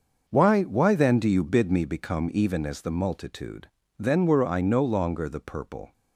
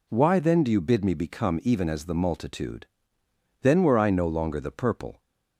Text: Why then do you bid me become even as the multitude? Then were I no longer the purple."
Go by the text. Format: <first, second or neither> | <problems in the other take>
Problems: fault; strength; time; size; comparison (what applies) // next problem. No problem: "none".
second | starts louder than the rest; noticeable; until 1.2 s; 6 dB // says "Why" twice; at 0.6 s